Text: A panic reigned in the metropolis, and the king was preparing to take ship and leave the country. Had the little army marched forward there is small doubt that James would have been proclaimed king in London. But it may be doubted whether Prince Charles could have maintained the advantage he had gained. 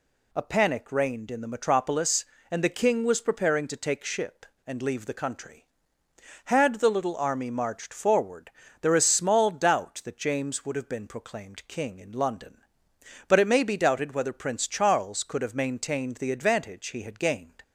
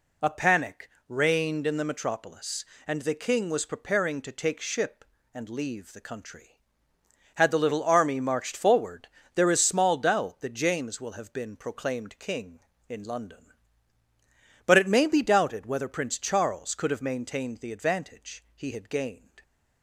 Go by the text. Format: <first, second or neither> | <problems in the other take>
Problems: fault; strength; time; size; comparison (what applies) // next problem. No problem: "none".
first | pauses between "panic" and "reigned"; slight; at 0.8 s; 0.18 s long // pauses between "forward" and "there"; slight; at 9.0 s; 0.28 s long; slight in the first // says "will" for "would"; at 10.9 s